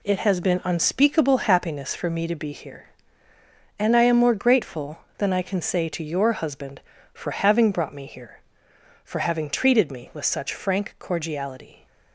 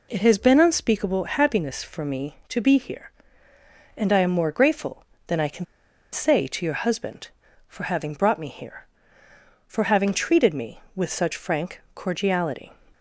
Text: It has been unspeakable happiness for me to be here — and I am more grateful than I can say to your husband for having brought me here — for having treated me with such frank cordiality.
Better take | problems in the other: first | pauses between "can" and "say"; noticeable; at 5.6 s; 0.47 s long

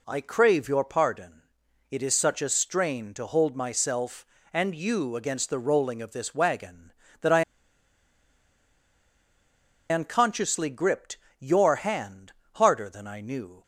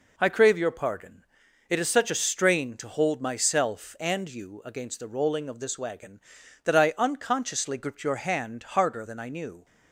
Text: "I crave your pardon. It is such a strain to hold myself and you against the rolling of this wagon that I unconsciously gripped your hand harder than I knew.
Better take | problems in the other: second | pauses between "I" and "unconsciously"; strong; at 7.4 s; 2.4 s long // pauses between "gripped" and "your"; slight; at 11.1 s; 0.22 s long // pauses between "hand" and "harder"; slight; at 12.3 s; 0.22 s long

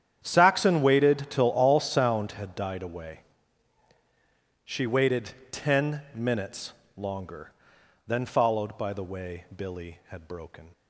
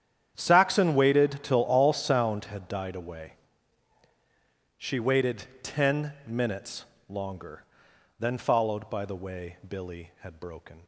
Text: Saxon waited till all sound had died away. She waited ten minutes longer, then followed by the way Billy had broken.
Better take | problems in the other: neither | starts louder than the rest; strong; the same in both // pauses between "waited" and "ten"; slight; the same in both // pauses between "minutes" and "longer"; slight; the same in both

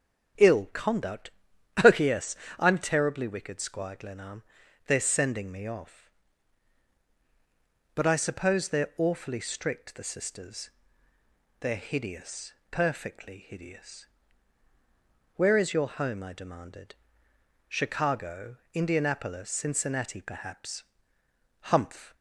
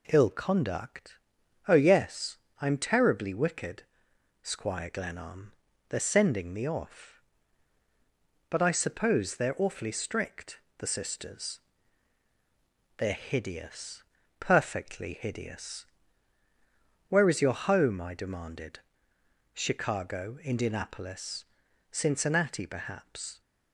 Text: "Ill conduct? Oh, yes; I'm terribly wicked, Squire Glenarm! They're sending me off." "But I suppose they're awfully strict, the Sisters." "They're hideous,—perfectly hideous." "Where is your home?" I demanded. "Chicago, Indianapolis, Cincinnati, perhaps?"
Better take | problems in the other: second | starts louder than the rest; strong; until 2.0 s; 9 dB // goes on to say "Humph"; from 21.6 s on; 0.54 s long

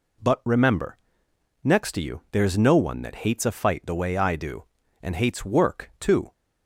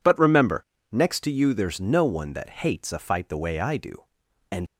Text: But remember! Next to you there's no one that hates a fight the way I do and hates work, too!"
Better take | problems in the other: first | stops before "hates work too"; at 4.6 s

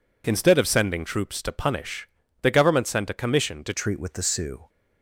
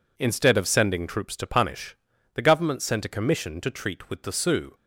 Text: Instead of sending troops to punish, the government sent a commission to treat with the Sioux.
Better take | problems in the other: second | changes voice at "treat"; from 3.7 s on; 0.9 s long

